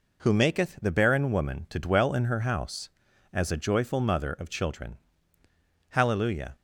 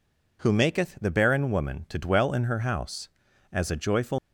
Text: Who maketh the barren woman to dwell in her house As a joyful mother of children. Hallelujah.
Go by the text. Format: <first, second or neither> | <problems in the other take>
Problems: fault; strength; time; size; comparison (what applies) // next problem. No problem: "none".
first | stops before "mother of children Hallelujah"; at 4.1 s